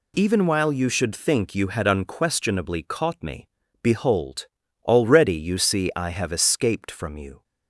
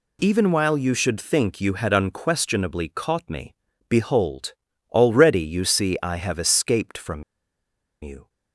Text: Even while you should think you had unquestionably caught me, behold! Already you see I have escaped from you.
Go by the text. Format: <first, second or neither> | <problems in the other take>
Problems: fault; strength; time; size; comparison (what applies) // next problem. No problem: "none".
first | pauses between "from" and "you"; noticeable; at 7.2 s; 0.79 s long